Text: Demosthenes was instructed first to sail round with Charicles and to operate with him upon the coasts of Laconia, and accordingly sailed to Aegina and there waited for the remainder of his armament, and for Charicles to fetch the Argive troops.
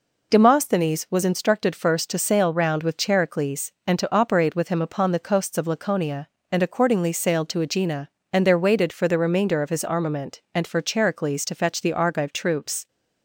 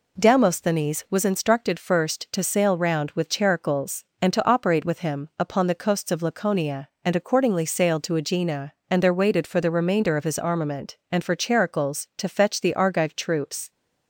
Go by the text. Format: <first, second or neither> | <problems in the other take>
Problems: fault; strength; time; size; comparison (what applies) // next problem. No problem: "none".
neither | none